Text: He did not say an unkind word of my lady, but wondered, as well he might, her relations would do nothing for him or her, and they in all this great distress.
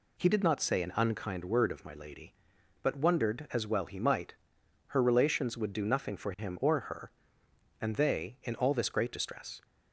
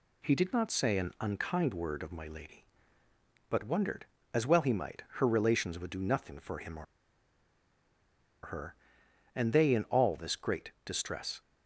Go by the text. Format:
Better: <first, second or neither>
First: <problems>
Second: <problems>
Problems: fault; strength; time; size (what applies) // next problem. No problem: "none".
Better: first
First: none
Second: pauses between "or" and "her"; strong; at 6.8 s; 1.5 s long